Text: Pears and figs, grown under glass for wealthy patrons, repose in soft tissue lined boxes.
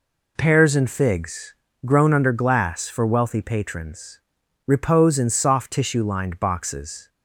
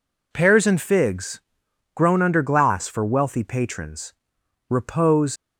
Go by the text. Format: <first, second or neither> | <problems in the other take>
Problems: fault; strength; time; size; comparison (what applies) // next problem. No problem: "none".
first | stops before "in soft tissue lined boxes"; at 5.3 s